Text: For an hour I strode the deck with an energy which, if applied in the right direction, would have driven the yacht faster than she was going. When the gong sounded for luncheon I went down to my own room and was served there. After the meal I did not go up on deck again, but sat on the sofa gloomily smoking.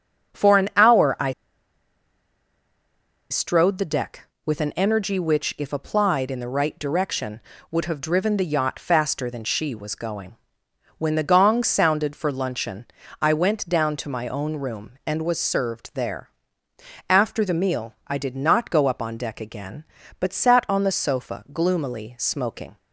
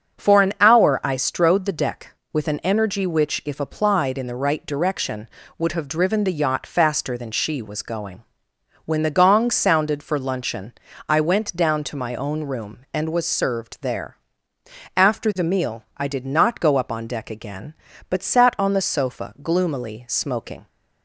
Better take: second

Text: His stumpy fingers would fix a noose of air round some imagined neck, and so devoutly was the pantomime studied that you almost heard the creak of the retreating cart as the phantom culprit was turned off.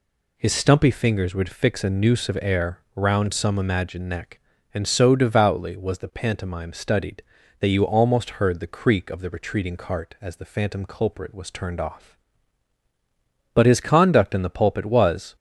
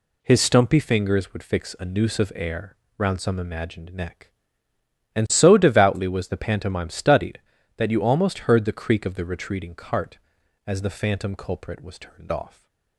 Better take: second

